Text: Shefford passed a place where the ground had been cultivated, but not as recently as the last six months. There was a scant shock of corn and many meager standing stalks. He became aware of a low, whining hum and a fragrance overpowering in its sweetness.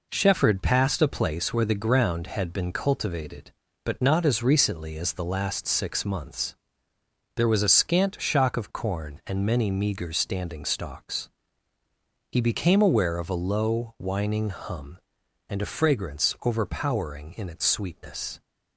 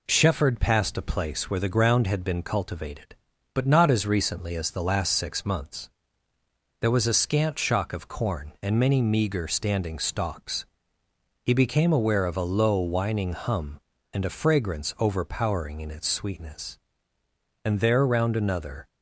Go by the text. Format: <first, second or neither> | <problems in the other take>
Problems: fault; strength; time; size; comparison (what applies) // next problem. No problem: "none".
first | goes on to say "And there round another"; noticeable; from 17.6 s on; 1.2 s long